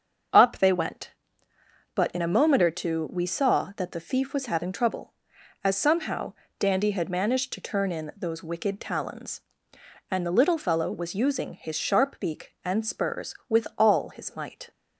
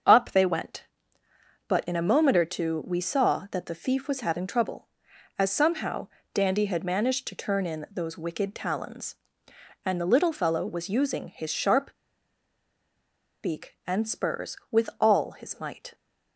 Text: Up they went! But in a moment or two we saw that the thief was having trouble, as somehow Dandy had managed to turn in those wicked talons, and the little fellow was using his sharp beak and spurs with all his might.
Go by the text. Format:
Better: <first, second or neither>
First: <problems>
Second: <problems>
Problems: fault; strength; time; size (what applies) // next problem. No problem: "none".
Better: first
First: starts louder than the rest; until 2.2 s; 7 dB // pauses between "somehow" and "Dandy"; slight; at 6.3 s; 0.26 s long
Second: starts louder than the rest; until 1.9 s; 7 dB // pauses between "somehow" and "Dandy"; slight; at 6.0 s; 0.26 s long // pauses between "sharp" and "beak"; strong; at 11.9 s; 1.4 s long